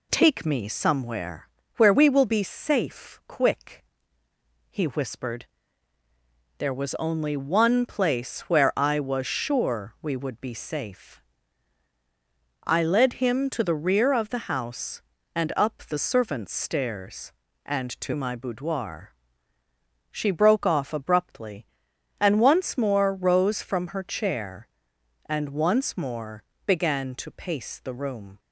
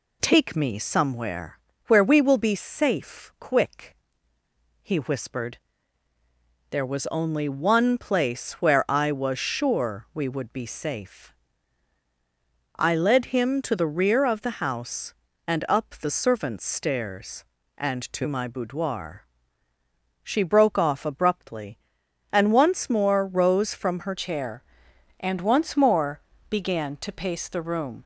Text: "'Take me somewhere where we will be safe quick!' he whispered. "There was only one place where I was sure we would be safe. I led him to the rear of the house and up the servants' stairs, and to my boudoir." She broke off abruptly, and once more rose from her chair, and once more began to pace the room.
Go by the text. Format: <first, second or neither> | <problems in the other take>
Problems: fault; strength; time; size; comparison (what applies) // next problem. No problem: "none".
first | pauses between "somewhere" and "where"; slight; at 1.5 s; 0.30 s long; slight in the first // changes voice at "chair"; from 24.1 s on; 3.9 s long // pauses between "more" and "began"; slight; at 26.2 s; 0.28 s long; slight in the first